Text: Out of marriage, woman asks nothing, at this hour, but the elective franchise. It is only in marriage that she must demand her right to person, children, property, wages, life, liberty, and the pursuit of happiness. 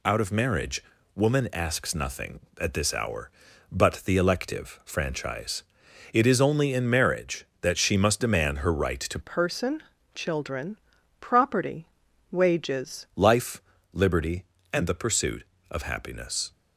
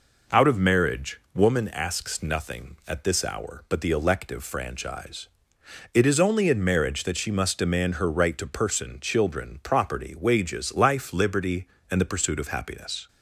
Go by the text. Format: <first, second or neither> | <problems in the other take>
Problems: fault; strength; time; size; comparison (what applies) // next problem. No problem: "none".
second | changes voice from "person" to "wages"; from 9.2 to 13.0 s; 3.8 s long